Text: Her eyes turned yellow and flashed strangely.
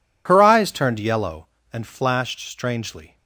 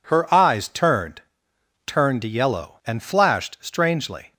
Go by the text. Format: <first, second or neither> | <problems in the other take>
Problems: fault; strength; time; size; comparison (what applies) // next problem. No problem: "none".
first | says "turned" twice; at 1.8 s